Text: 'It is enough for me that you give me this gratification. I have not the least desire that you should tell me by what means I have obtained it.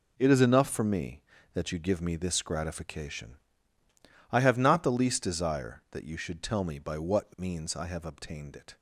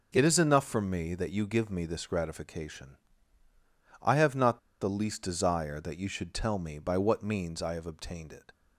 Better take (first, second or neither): first